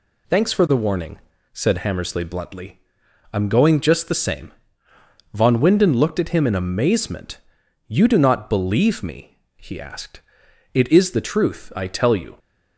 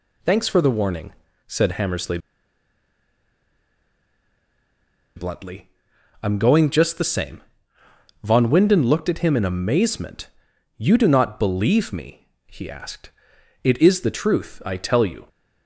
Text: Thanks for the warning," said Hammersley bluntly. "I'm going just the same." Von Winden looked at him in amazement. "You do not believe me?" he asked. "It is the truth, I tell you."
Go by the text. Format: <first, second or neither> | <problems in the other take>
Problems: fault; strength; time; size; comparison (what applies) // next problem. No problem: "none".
first | pauses between "Hammersley" and "bluntly"; strong; at 2.1 s; 2.9 s long